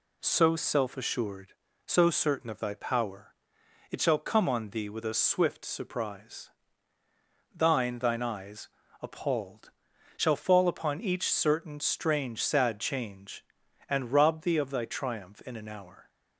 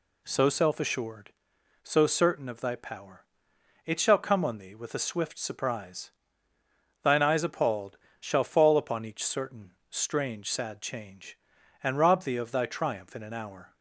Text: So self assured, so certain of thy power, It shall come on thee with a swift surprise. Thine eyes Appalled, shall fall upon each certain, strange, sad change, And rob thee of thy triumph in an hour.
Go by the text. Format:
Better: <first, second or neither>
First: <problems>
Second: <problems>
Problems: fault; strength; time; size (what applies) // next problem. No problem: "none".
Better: second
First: says "Thine" twice; at 8.0 s // pauses between "eyes" and "Appalled"; slight; at 8.6 s; 0.34 s long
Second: none